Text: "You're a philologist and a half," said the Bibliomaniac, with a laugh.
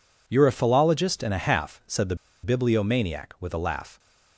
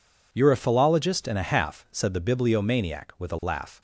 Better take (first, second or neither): second